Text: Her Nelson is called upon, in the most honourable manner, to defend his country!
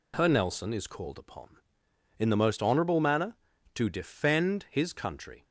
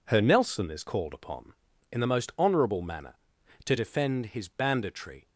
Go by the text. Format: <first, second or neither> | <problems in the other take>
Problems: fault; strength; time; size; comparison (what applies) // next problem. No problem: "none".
first | says "banditry" for "country"; at 4.4 s